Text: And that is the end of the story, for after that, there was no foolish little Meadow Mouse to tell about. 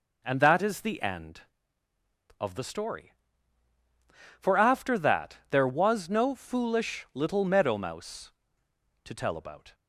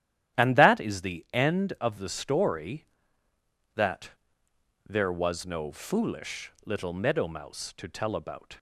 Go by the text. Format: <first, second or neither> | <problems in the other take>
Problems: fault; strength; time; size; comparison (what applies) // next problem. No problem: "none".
first | starts louder than the rest; strong; until 1.4 s; 11.5 dB // skips "for after"; at 3.3 s